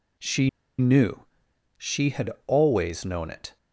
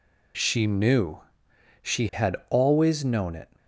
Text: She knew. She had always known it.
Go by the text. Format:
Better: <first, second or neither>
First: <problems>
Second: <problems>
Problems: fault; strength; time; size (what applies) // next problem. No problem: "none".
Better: second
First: pauses between "She" and "knew"; slight; at 0.4 s; 0.29 s long // pauses between "had" and "always"; slight; at 2.3 s; 0.16 s long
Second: none